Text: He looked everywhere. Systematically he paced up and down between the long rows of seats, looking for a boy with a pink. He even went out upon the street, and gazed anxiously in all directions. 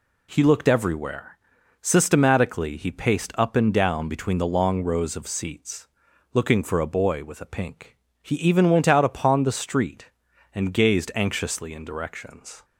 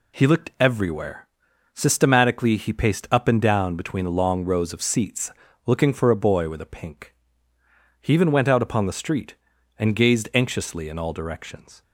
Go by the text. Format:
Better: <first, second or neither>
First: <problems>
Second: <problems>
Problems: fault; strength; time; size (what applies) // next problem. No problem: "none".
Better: second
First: skips "all"; at 11.8 s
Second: none